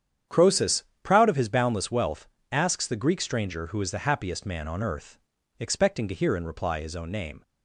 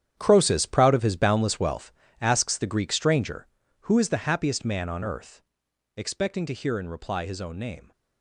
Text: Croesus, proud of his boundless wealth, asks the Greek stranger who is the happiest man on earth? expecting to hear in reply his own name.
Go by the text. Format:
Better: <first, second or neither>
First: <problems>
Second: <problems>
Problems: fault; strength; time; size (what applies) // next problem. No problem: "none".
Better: first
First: starts louder than the rest; strong; until 1.4 s; 9 dB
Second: gets quieter; strong; throughout; 13.5 dB // starts louder than the rest; strong; until 1.2 s; 9.5 dB